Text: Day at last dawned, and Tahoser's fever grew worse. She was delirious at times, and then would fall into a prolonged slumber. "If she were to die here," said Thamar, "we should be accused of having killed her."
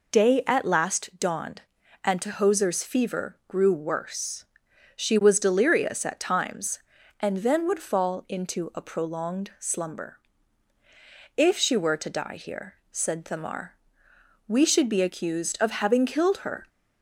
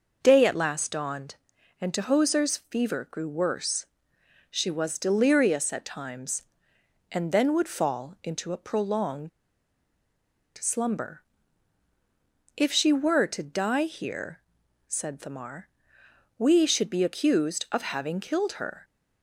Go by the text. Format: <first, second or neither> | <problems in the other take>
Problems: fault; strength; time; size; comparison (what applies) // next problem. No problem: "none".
first | pauses between "prolonged" and "slumber"; strong; at 9.2 s; 1.2 s long